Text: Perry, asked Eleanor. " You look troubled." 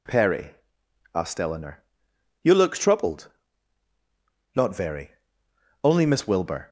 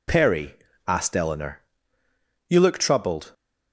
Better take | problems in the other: second | goes on to say "Not very only Miss Wilbur"; strong; from 4.5 s on; 2.1 s long

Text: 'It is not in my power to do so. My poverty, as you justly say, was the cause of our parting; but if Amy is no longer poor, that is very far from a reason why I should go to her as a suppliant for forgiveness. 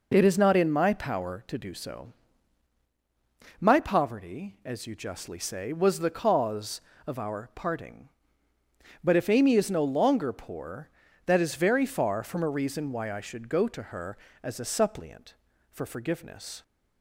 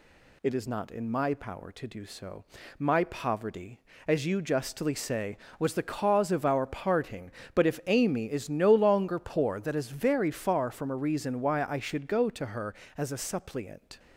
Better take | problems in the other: first | stops before "for forgiveness"; at 13.9 s

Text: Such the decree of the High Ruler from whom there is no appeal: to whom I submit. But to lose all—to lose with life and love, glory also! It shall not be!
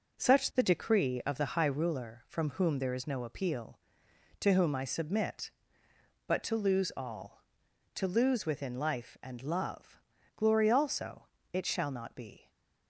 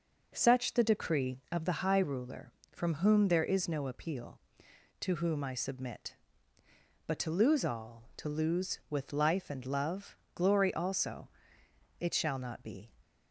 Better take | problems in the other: second | says "within" for "with"; at 8.4 s // stays silent after the last word; slight; from 12.3 s on; 0.5 s long

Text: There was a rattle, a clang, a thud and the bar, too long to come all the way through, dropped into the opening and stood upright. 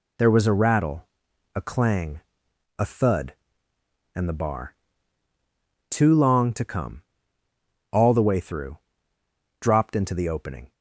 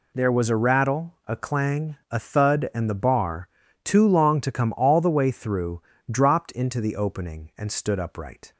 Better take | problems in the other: second | pauses between "come" and "all"; noticeable; at 7.0 s; 0.90 s long // stops before "and stood upright"; at 10.7 s

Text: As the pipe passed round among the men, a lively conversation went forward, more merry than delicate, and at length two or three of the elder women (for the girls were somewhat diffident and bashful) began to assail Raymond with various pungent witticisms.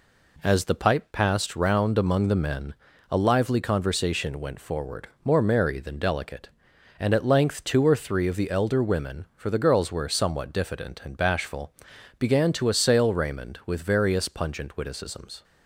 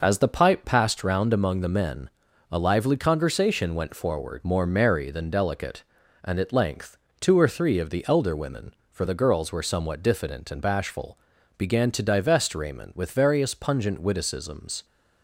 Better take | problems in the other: first | pauses between "length" and "two"; slight; at 6.9 s; 0.22 s long // says "divest" for "assail"; at 12.0 s

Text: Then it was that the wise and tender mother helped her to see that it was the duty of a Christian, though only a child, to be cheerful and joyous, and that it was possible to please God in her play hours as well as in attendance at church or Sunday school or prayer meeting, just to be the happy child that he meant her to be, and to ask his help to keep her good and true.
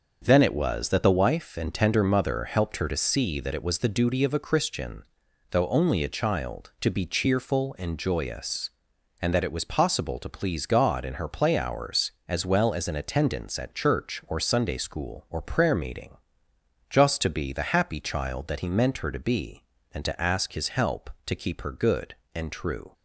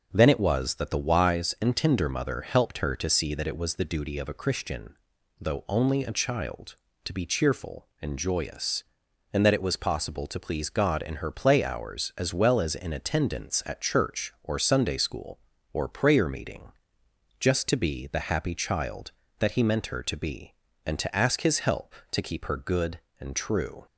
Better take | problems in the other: second | starts louder than the rest; until 1.2 s; 6 dB; also in the second // says "wife" for "wise"; at 1.1 s

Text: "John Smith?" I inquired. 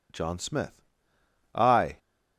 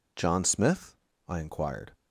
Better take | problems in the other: second | stops before "inquired"; at 1.9 s

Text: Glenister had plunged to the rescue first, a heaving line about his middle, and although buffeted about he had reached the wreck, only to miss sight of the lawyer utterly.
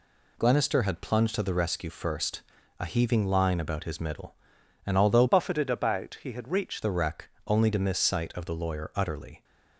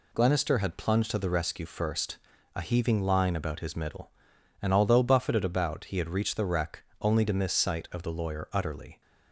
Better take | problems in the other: second | changes voice from "buffeted" to "reached"; from 5.2 to 6.8 s; 1.6 s long

